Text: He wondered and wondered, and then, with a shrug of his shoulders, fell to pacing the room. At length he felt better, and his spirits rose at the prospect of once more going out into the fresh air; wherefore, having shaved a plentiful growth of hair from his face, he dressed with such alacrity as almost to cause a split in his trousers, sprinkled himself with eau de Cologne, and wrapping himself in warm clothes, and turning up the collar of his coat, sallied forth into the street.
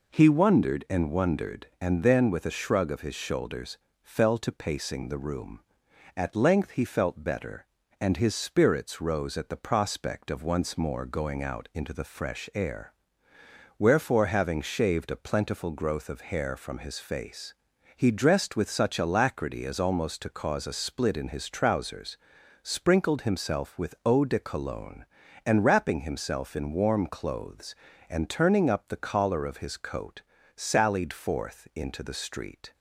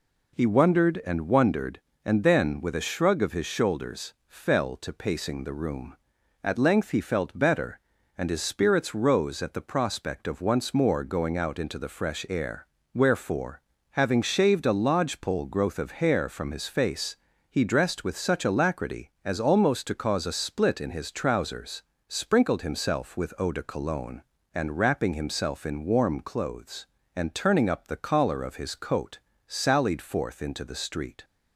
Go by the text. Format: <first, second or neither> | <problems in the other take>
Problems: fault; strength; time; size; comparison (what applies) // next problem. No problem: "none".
first | says "lodgepole" for "plentiful"; at 14.7 s